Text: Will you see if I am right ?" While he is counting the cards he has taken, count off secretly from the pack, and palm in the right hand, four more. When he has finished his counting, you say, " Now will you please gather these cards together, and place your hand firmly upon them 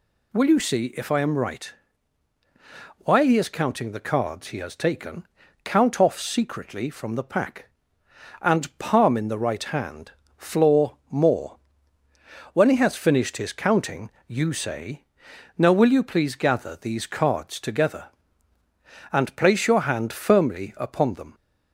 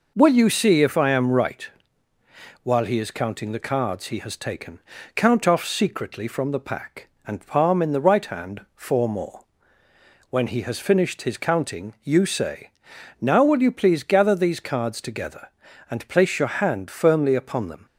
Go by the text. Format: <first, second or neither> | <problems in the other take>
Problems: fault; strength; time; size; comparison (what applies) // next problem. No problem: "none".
second | says "floor" for "four"; at 10.3 s